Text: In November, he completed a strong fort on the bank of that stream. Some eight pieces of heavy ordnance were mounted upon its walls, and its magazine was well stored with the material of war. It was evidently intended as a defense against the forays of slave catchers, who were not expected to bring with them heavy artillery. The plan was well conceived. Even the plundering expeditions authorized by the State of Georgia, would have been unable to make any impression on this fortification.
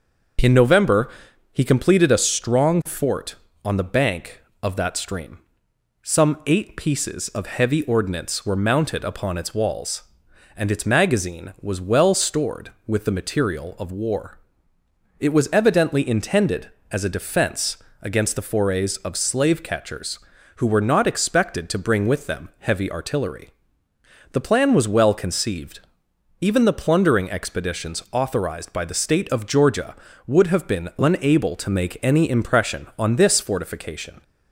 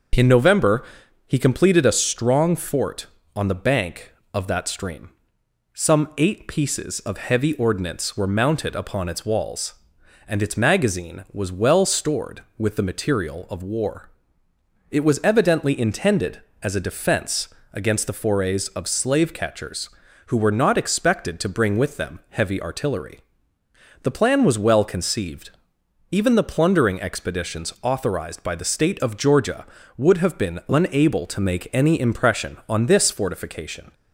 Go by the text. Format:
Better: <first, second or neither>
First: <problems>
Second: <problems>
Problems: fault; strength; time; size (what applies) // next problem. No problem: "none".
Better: neither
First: starts louder than the rest; noticeable; until 1.8 s; 6 dB // pauses between "defense" and "against"; slight; at 17.7 s; 0.24 s long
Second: starts louder than the rest; noticeable; until 1.5 s; 6 dB // pauses between "defense" and "against"; slight; at 17.4 s; 0.24 s long